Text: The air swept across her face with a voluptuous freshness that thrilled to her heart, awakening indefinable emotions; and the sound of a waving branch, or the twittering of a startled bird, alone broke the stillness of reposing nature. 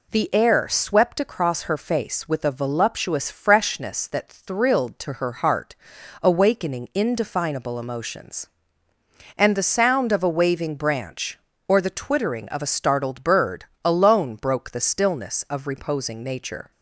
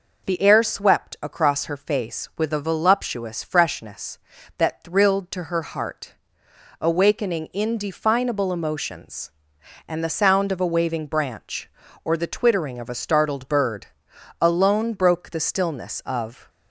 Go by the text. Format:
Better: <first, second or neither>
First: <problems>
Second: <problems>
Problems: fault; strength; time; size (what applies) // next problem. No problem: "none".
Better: first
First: none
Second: stops before "reposing nature"; at 16.4 s